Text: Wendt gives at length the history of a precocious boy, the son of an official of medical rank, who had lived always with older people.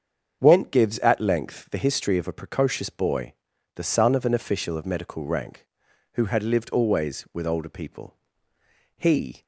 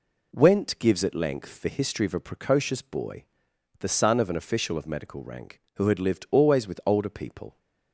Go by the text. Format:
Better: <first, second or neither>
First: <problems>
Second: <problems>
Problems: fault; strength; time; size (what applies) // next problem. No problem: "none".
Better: second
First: starts louder than the rest; strong; until 1.4 s; 7 dB // goes on to say "He"; slight; from 8.9 s on; 0.44 s long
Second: none